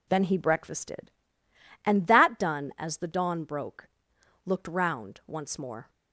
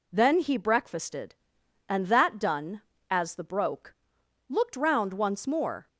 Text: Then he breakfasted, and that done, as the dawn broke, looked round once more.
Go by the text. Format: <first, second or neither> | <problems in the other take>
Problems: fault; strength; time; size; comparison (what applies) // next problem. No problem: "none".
first | skips "dawn"; at 3.4 s